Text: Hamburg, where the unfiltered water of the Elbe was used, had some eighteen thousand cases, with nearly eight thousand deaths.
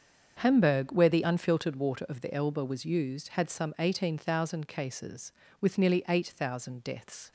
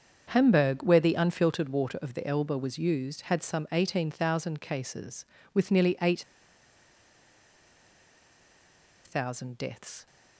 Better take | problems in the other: first | starts louder than the rest; strong; until 1.3 s; 7 dB; strong in the first // pauses between "eight" and "thousand"; strong; at 6.2 s; 2.8 s long

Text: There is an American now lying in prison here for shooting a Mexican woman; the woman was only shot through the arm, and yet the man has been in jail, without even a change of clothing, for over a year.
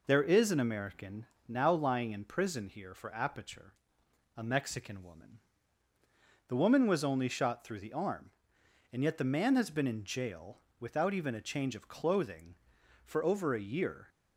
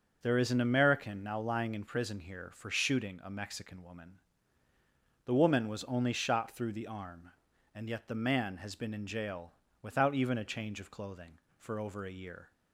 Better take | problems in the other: second | pauses between "American" and "now"; slight; at 1.2 s; 0.20 s long // says "aperture" for "shooting"; at 3.1 s

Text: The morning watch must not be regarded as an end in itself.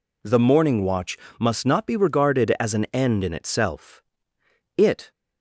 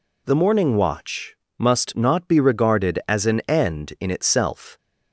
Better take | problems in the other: second | pauses between "watch" and "must"; slight; at 1.1 s; 0.22 s long; slight in the second // goes on to say "It"; slight; from 4.7 s on; 0.34 s long

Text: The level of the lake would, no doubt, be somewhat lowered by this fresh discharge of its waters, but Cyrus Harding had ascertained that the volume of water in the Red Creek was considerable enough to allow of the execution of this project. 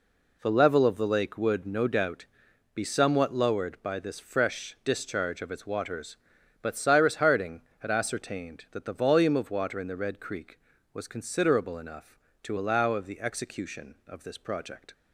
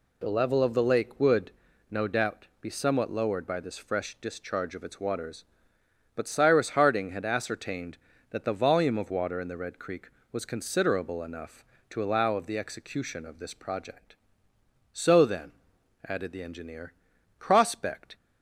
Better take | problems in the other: first | goes on to say "So then added the engineer Prospect"; strong; from 14.9 s on; 3.2 s long

